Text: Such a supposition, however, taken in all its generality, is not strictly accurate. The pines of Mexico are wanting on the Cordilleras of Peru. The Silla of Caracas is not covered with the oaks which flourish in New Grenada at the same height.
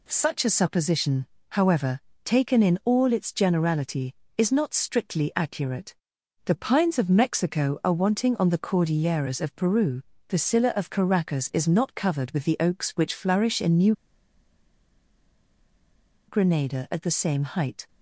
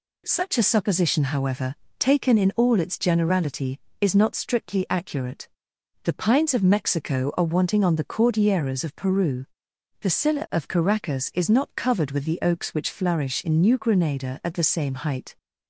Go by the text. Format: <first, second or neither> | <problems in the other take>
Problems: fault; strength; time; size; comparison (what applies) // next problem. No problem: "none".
second | pauses between "New" and "Grenada"; strong; at 13.9 s; 2.3 s long